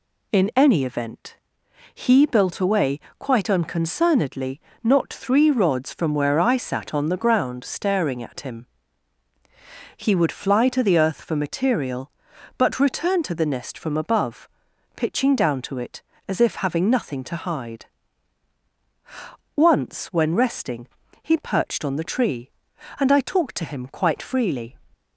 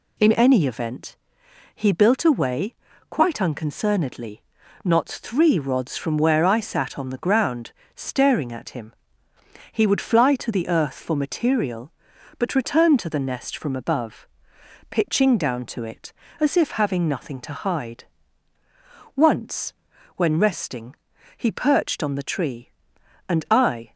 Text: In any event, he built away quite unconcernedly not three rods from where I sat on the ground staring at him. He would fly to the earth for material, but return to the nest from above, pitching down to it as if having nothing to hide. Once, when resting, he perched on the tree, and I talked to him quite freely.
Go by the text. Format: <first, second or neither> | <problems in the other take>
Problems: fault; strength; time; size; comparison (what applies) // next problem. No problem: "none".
first | pauses between "away" and "quite"; slight; at 2.7 s; 0.36 s long; slight in the first // pauses between "unconcernedly" and "not"; at 4.4 s; 0.42 s long; slight in the first // pauses between "ground" and "staring"; slight; at 7.7 s; 0.22 s long // stops before "talked to him quite freely"; at 23.9 s